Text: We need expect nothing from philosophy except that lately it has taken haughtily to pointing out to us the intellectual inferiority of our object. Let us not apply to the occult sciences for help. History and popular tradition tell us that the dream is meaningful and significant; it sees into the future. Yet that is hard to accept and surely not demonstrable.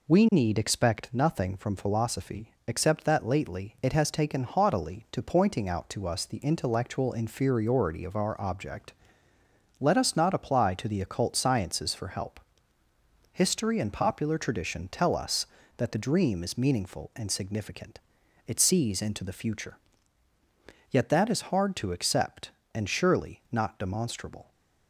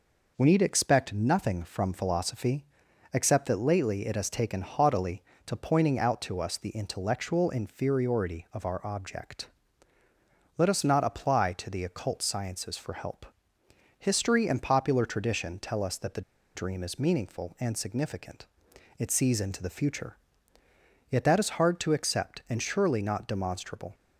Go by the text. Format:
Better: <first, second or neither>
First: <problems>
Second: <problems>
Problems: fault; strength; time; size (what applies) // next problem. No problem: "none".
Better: first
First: pauses between "philosophy" and "except"; slight; at 2.5 s; 0.16 s long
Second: pauses between "philosophy" and "except"; noticeable; at 2.6 s; 0.48 s long // pauses between "the" and "dream"; slight; at 16.2 s; 0.34 s long